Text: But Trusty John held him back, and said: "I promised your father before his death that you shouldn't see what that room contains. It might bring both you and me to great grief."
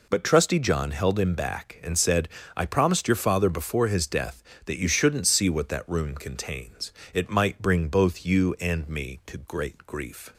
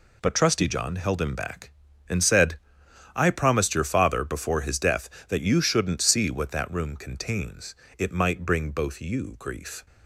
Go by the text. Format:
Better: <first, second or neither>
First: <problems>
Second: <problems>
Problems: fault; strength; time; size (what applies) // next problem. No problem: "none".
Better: first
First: none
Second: skips "and me to great"; at 9.3 s